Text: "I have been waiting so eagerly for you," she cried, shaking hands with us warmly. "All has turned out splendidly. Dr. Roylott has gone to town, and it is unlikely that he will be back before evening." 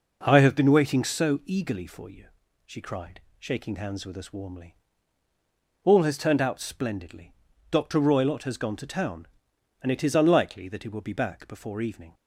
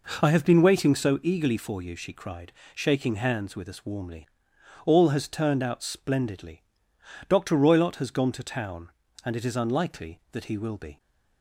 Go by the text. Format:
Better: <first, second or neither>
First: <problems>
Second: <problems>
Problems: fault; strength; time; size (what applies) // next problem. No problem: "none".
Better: first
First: none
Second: stops before "back before evening"; at 10.9 s